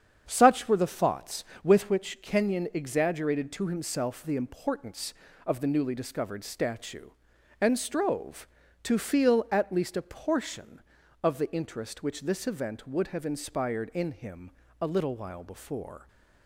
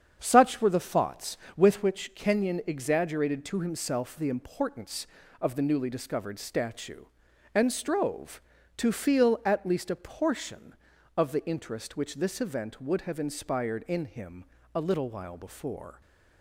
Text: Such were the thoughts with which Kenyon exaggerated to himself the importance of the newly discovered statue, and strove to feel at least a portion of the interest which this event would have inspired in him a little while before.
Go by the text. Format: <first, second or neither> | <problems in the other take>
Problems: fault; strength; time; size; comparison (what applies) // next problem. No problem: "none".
neither | starts louder than the rest; strong; the same in both // pauses between "him" and "a"; slight; the same in both